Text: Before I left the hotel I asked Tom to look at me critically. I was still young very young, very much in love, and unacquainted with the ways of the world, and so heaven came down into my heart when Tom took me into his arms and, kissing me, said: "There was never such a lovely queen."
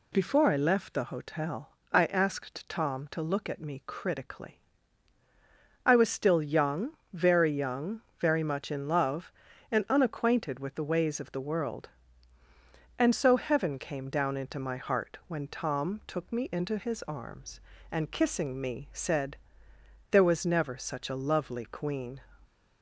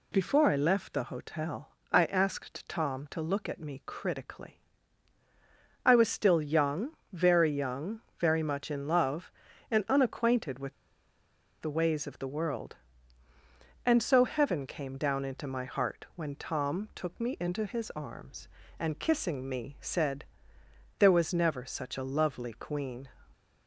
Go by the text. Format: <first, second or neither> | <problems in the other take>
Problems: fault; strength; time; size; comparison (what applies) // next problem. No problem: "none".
first | pauses between "hotel" and "I"; slight; at 1.7 s; 0.20 s long; slight in the first // pauses between "young" and "very"; slight; at 6.9 s; 0.20 s long; slight in the first // pauses between "with" and "the"; noticeable; at 10.7 s; 0.87 s long